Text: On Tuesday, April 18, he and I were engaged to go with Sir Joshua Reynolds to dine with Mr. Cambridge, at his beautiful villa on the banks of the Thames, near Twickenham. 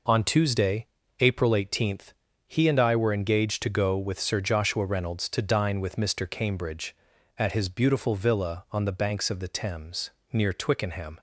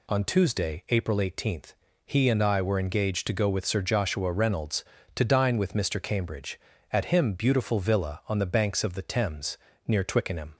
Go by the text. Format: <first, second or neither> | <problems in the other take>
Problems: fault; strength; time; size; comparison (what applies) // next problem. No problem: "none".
first | says "him" for "his"; at 7.0 s